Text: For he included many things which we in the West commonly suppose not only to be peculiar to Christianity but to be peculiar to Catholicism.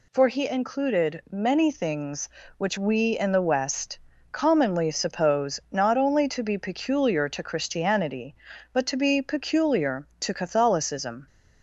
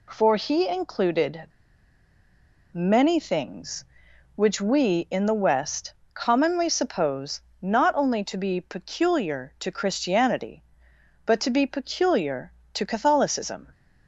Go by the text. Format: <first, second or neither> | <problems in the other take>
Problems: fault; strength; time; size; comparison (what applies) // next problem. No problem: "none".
first | pauses between "included" and "many"; strong; at 1.4 s; 1.2 s long // pauses between "West" and "commonly"; slight; at 5.9 s; 0.22 s long; slight in the first // pauses between "suppose" and "not"; slight; at 7.3 s; 0.22 s long